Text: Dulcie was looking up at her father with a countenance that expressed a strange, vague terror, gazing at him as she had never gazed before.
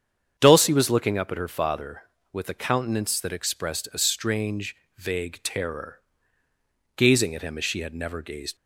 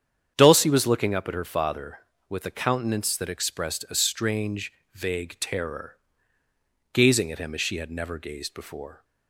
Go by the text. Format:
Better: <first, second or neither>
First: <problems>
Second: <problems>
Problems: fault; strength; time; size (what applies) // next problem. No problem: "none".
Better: second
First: starts louder than the rest; strong; until 1.4 s; 8 dB // stops before "before"; at 8.5 s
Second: starts louder than the rest; strong; until 1.3 s; 8.5 dB